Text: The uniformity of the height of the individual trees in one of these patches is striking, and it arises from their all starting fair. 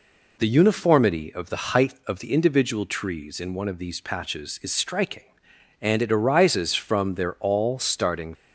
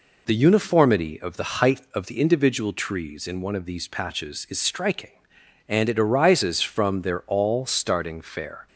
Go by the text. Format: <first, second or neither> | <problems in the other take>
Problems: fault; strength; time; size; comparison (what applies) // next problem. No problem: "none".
second | stops before "fair"; at 8.3 s